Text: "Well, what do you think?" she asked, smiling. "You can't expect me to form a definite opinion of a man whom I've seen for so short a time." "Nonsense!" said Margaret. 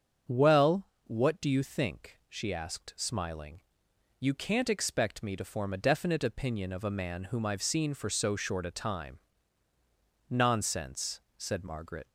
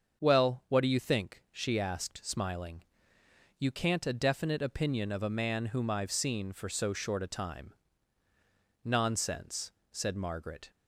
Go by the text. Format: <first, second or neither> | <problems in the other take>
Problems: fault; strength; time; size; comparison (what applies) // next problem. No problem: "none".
first | starts louder than the rest; until 1.2 s; 6.5 dB; strong in the first // skips "expect me to form"; at 4.0 s